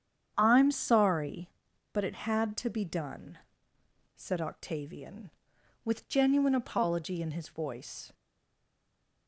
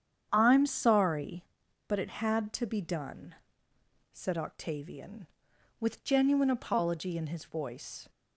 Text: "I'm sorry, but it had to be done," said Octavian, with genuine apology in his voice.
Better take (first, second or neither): second